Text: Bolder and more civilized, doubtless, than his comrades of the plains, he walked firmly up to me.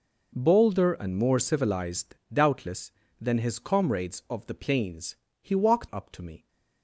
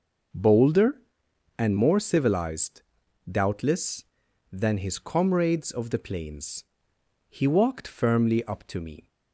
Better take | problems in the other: second | skips "firmly"; at 5.9 s

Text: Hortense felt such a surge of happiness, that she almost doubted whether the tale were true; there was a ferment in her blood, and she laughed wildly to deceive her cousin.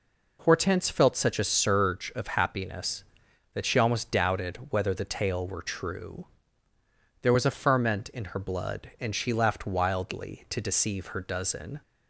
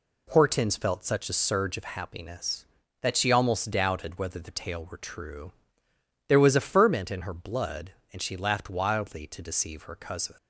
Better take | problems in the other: second | says "dozen" for "cousin"; at 11.1 s

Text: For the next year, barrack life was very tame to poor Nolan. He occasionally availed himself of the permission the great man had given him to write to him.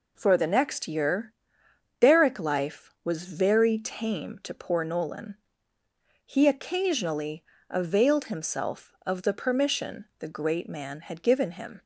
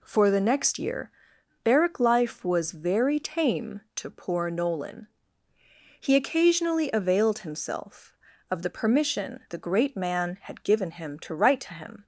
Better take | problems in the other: second | pauses between "occasionally" and "availed"; slight; at 7.4 s; 0.24 s long // stops before "to write to him"; at 11.8 s

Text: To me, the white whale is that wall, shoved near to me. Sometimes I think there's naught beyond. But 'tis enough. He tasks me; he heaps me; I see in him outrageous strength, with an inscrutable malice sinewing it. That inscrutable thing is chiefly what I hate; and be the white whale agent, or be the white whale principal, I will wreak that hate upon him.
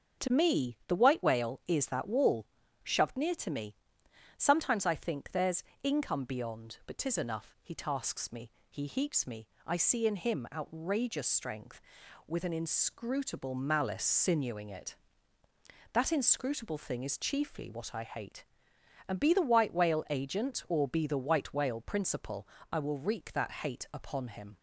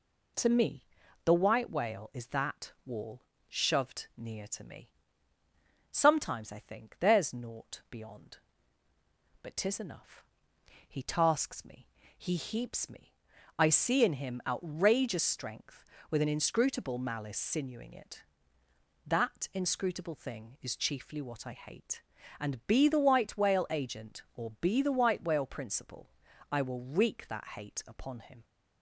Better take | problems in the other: second | starts louder than the rest; until 1.3 s; 6.5 dB // says "income" for "naught"; at 5.8 s

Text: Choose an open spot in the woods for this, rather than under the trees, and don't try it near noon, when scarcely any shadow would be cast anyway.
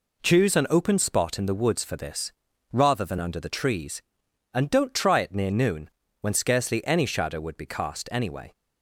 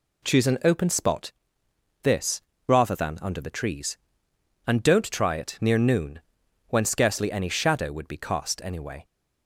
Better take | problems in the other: first | skips "in the woods for"; at 1.6 s

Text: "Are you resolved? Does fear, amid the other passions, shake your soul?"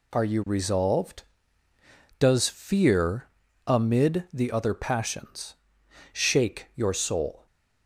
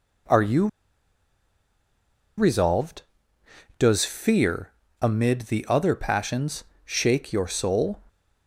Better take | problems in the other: first | pauses between "you" and "resolved"; strong; at 0.6 s; 1.7 s long

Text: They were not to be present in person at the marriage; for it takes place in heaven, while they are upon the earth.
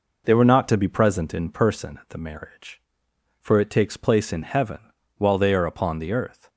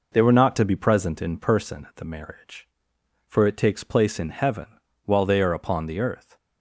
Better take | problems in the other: neither | none

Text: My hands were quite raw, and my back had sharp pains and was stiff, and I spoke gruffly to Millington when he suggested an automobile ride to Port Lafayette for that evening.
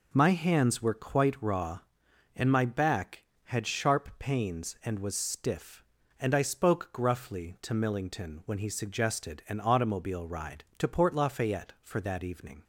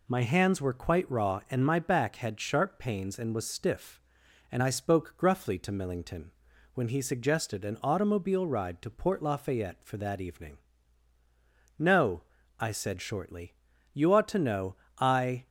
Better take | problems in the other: first | pauses between "Millington" and "when"; at 6.3 s; 0.44 s long // goes on to say "No I said shortly You ought to know I"; strong; from 11.7 s on; 3.7 s long

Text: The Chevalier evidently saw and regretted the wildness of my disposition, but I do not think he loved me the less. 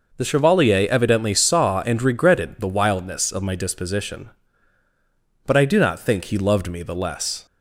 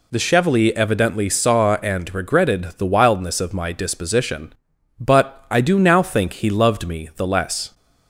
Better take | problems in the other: first | says "now" for "not"; at 5.7 s

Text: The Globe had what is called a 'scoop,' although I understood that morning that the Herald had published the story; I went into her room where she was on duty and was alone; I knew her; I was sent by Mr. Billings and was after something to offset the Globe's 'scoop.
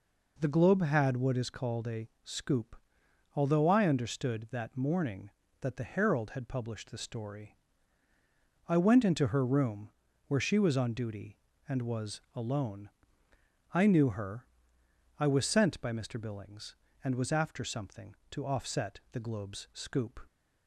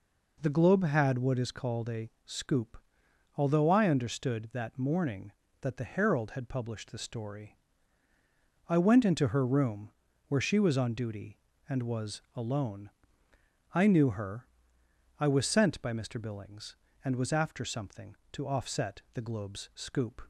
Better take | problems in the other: neither | pauses between "room" and "where"; slight; the same in both

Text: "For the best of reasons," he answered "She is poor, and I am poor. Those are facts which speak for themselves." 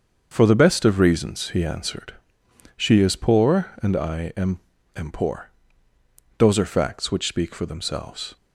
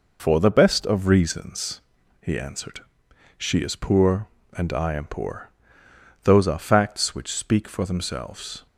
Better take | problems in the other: second | starts louder than the rest; until 1.3 s; 6.5 dB // pauses between "answered" and "She"; noticeable; at 2.1 s; 0.64 s long; noticeable in the second // says "am" twice; at 4.9 s

